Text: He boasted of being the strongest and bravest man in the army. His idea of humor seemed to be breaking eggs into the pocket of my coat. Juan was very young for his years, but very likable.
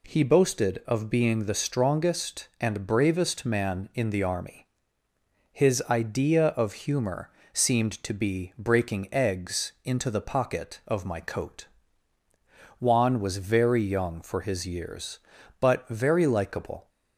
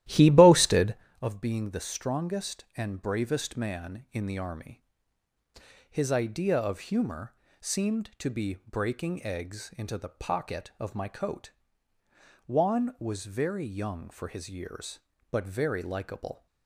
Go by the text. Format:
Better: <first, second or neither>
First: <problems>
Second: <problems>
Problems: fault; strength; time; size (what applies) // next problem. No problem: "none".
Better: first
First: pauses between "humor" and "seemed"; slight; at 7.3 s; 0.24 s long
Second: starts louder than the rest; strong; until 1.1 s; 14 dB // pauses between "humor" and "seemed"; slight; at 7.3 s; 0.26 s long